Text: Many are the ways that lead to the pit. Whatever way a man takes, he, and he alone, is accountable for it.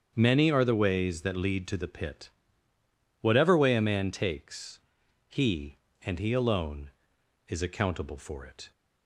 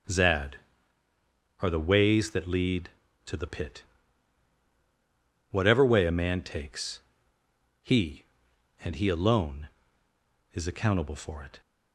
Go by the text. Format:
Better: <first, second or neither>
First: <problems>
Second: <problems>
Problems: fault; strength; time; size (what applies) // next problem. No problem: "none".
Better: first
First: starts louder than the rest; strong; until 1.1 s; 7.5 dB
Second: starts louder than the rest; strong; until 2.1 s; 7.5 dB // says "Zad" for "Many"; at 0.0 s